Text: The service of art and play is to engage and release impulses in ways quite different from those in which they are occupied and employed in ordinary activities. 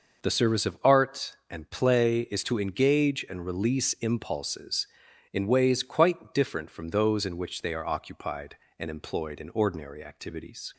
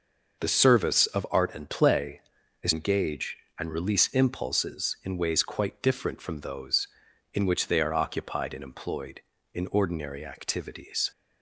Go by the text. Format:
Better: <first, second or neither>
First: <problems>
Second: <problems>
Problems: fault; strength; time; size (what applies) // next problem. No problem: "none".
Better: first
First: none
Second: skips "to"; at 2.7 s